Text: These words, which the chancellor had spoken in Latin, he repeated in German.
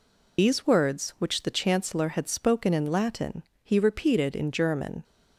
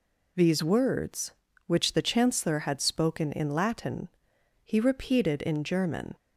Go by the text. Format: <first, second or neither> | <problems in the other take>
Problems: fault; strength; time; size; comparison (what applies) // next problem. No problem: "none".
second | loses the start of "These"; at 0.3 s; 55 ms